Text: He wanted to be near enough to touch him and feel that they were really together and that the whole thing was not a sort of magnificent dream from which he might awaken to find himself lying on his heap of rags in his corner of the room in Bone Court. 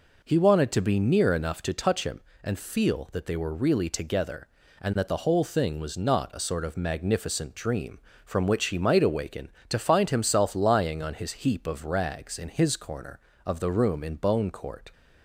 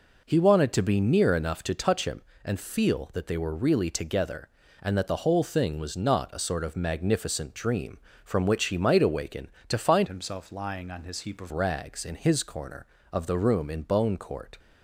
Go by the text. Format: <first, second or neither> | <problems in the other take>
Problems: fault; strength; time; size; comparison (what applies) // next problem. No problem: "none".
first | changes voice from "himself" to "of"; from 10.0 to 11.5 s; 1.5 s long